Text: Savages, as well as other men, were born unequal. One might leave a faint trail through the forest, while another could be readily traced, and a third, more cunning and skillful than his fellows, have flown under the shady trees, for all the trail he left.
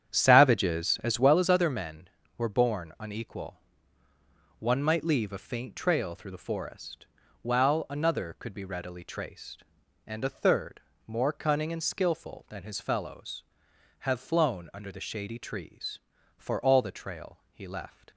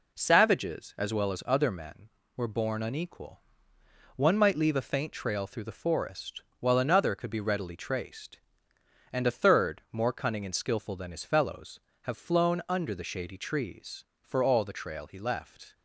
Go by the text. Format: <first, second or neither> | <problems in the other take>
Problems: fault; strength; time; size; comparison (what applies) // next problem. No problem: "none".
second | starts louder than the rest; strong; until 1.5 s; 9 dB